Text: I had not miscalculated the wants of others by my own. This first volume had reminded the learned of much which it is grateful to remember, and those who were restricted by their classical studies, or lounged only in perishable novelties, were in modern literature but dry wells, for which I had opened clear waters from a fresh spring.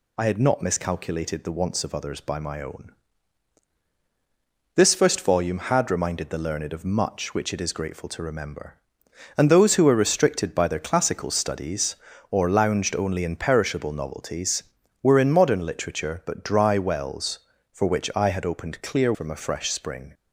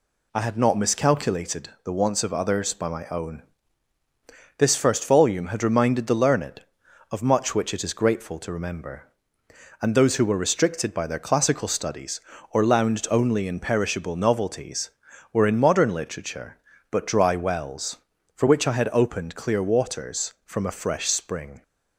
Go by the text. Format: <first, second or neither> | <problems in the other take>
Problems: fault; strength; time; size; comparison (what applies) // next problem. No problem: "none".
second | skips "waters"; at 19.1 s